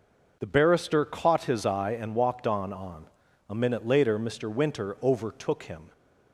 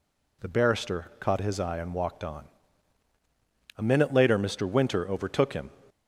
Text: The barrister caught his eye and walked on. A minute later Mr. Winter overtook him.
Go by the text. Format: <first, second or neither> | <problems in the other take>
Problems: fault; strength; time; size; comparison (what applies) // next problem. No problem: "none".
second | says "on" twice; at 2.7 s